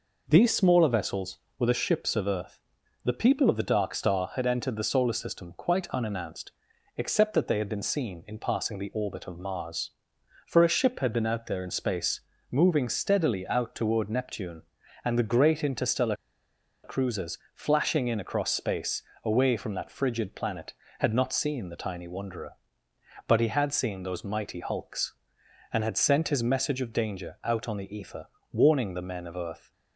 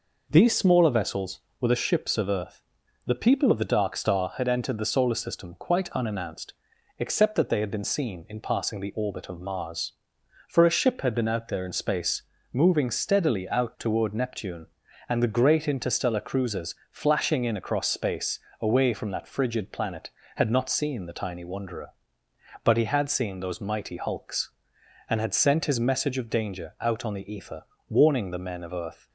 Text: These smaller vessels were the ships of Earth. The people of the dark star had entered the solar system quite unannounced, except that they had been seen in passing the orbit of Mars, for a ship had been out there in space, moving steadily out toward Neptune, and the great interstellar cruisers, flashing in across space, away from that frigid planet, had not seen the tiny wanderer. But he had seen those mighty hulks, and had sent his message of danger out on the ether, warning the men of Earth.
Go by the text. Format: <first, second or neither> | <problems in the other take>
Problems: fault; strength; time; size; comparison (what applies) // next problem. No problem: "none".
second | pauses between "interstellar" and "cruisers"; noticeable; at 16.1 s; 0.67 s long